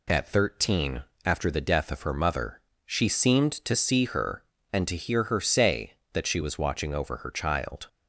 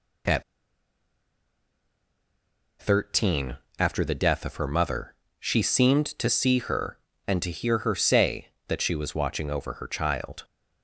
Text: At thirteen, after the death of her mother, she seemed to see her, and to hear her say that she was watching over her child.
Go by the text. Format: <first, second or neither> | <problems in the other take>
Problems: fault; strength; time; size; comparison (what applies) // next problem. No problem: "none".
first | pauses between "At" and "thirteen"; strong; at 0.4 s; 2.3 s long